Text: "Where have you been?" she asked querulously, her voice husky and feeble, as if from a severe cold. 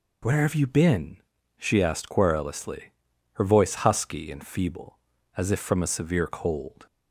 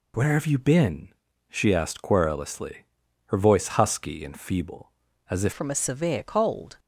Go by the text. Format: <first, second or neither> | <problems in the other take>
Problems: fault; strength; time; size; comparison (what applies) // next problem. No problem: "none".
first | changes voice at "from"; from 5.5 s on; 1.2 s long